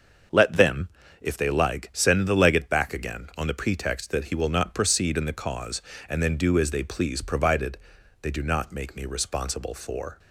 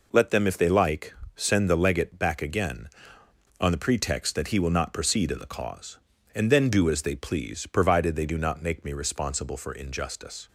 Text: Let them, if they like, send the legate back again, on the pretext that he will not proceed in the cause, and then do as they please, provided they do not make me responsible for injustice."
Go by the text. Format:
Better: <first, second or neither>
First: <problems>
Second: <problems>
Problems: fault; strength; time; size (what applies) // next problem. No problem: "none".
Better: second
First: starts louder than the rest; until 1.6 s; 6.5 dB // pauses between "provided" and "they"; noticeable; at 7.7 s; 0.46 s long // stops before "injustice"; at 10.1 s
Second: none